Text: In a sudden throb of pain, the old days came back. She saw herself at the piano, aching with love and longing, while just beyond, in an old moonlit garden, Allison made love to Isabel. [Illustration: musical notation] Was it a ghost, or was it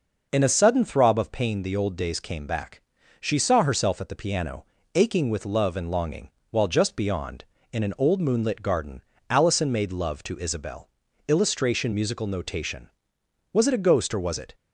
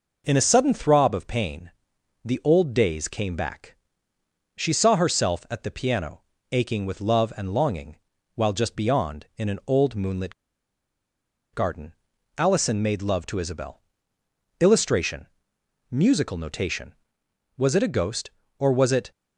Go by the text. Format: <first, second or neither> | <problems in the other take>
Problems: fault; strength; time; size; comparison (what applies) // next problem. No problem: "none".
first | pauses between "moonlit" and "garden"; at 10.3 s; 1.2 s long